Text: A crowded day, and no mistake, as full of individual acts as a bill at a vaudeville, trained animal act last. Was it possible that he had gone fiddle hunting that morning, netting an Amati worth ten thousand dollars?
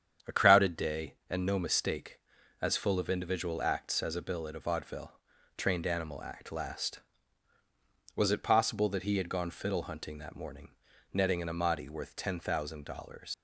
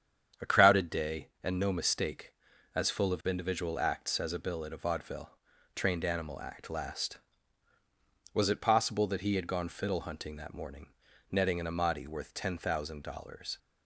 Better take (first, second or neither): second